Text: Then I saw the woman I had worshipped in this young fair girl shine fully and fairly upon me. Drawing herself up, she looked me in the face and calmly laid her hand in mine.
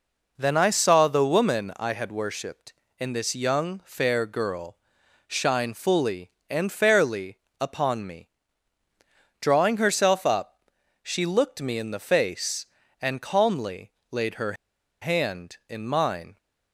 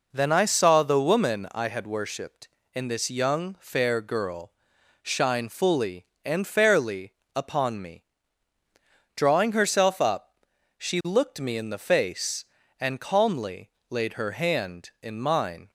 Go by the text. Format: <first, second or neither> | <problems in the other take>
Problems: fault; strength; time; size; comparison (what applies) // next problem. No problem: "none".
second | pauses between "girl" and "shine"; noticeable; at 4.7 s; 0.52 s long; noticeable in the second // pauses between "fairly" and "upon"; slight; at 7.3 s; 0.24 s long; slight in the second // pauses between "calmly" and "laid"; slight; at 13.9 s; 0.20 s long; slight in the second // pauses between "her" and "hand"; noticeable; at 14.5 s; 0.48 s long